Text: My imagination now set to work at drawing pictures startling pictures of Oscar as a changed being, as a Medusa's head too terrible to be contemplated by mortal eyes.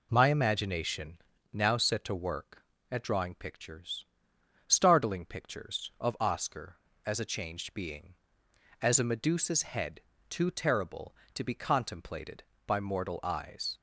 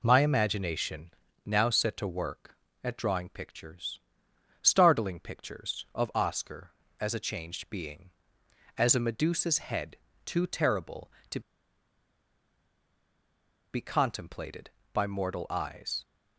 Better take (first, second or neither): first